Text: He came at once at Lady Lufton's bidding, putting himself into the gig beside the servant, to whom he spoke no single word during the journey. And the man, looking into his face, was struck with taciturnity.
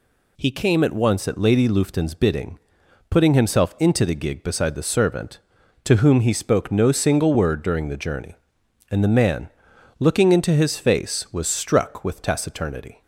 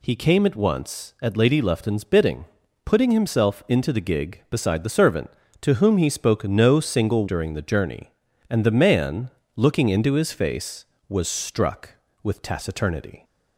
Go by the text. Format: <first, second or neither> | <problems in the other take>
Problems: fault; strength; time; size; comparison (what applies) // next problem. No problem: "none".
first | skips "word"; at 7.2 s